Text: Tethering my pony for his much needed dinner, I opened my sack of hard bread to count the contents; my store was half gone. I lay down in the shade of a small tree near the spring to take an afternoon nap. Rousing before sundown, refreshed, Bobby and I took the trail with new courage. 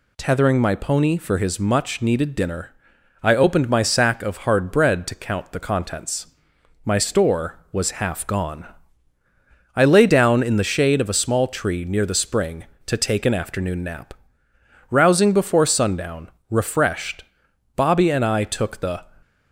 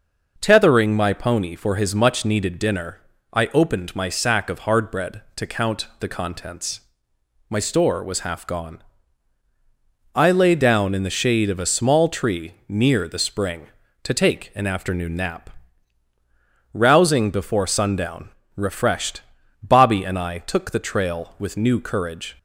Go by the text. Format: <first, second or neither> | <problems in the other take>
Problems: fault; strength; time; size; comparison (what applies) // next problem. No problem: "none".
second | stops before "trail with new courage"; at 19.2 s